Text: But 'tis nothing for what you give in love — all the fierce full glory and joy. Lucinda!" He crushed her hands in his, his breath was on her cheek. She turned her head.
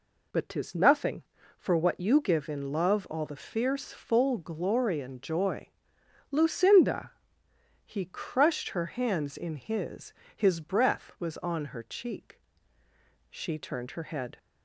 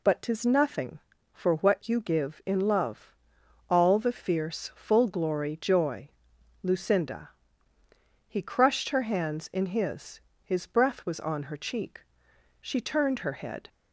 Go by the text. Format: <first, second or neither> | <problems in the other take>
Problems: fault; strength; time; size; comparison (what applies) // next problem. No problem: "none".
first | skips "and"; at 5.5 s